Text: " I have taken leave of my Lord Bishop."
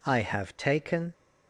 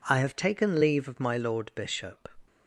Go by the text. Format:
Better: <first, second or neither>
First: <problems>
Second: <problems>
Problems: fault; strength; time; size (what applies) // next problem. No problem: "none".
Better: second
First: stops before "leave of my Lord Bishop"; at 1.1 s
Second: none